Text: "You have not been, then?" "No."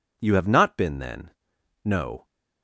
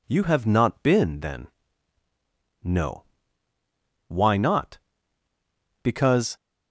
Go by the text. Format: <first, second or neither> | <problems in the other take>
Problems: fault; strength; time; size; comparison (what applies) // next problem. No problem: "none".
first | goes on to say "Why not Because"; strong; from 4.0 s on; 2.2 s long